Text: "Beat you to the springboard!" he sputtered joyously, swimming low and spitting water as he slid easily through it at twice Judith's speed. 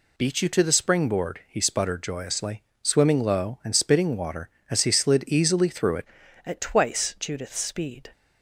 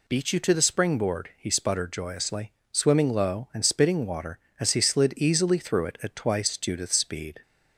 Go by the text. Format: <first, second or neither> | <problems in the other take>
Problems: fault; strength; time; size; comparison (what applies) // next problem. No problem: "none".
second | changes voice at "at"; from 6.4 s on; 1.7 s long